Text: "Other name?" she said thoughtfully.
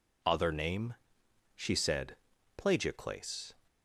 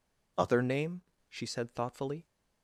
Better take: second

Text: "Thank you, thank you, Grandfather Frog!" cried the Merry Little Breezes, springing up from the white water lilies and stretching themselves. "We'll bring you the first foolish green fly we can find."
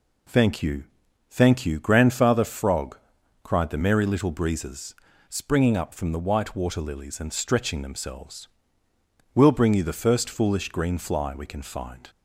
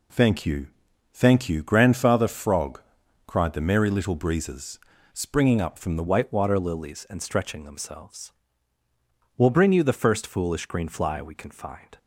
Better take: first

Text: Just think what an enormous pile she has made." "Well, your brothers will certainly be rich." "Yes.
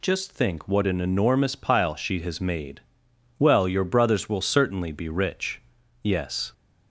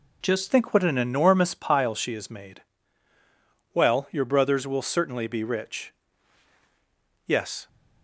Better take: first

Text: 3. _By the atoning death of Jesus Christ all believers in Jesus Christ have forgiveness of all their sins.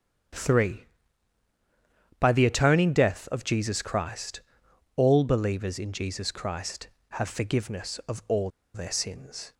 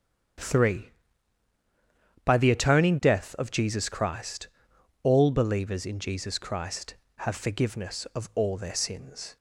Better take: second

